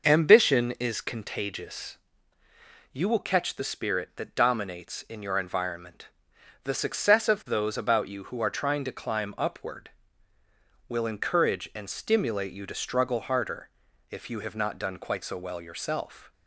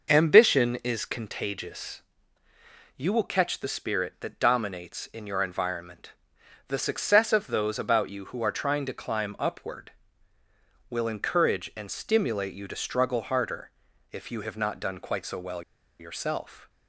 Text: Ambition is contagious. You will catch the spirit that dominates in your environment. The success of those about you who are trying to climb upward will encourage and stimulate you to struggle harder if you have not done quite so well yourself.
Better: first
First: pauses between "harder" and "if"; at 13.6 s; 0.42 s long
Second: pauses between "harder" and "if"; at 13.6 s; 0.42 s long // pauses between "well" and "yourself"; at 15.6 s; 0.38 s long

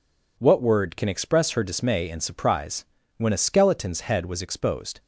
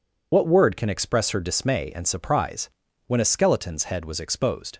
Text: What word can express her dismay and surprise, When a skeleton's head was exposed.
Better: first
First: none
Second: loses the start of "What"; at 0.3 s; 75 ms

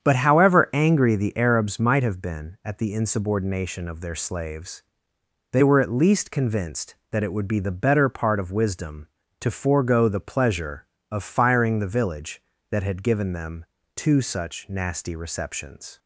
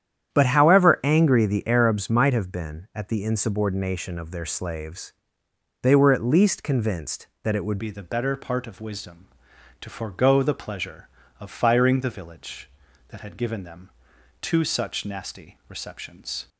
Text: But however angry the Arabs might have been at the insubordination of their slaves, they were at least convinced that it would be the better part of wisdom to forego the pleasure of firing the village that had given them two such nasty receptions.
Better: first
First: starts louder than the rest; strong; until 1.0 s; 8 dB // pauses between "them" and "two"; slight; at 13.6 s; 0.32 s long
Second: starts louder than the rest; strong; until 1.3 s; 9.5 dB // changes voice at "be"; from 7.7 s on; 8.7 s long // pauses between "them" and "two"; noticeable; at 13.9 s; 0.50 s long

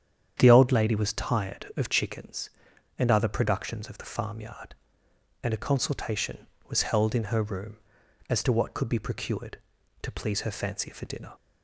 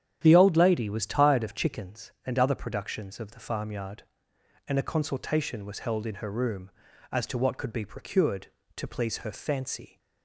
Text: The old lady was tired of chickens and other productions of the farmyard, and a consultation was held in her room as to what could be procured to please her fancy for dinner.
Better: first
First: starts louder than the rest; strong; until 1.3 s; 8.5 dB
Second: starts louder than the rest; strong; until 1.2 s; 9.5 dB // stops before "for dinner"; at 9.9 s

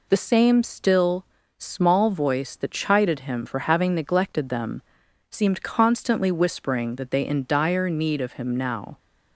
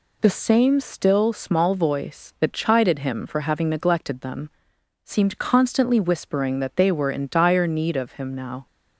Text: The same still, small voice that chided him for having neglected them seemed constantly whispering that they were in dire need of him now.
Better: second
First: pauses between "them" and "seemed"; noticeable; at 4.8 s; 0.48 s long // skips "were"; at 7.2 s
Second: pauses between "them" and "seemed"; noticeable; at 4.5 s; 0.52 s long

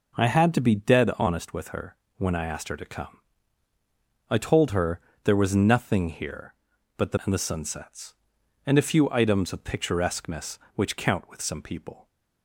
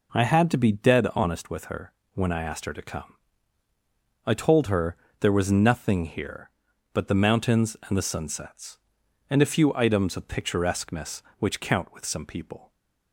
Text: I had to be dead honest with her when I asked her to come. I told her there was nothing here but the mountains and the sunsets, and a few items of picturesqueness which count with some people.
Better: second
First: pauses between "her" and "when"; slight; at 1.9 s; 0.22 s long // pauses between "her" and "there"; slight; at 5.0 s; 0.22 s long // skips "mountains"; at 7.1 s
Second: pauses between "her" and "when"; slight; at 1.9 s; 0.22 s long // pauses between "her" and "there"; slight; at 4.9 s; 0.22 s long

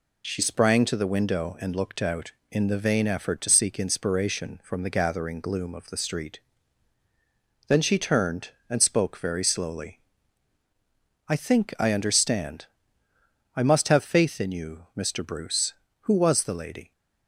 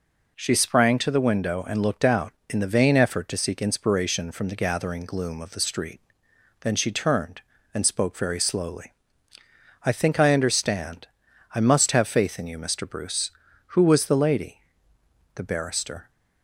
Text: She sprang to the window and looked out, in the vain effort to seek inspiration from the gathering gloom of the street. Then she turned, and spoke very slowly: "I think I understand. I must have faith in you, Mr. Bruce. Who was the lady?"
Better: first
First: none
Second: goes on to say "The barrister"; noticeable; from 15.3 s on; 0.74 s long

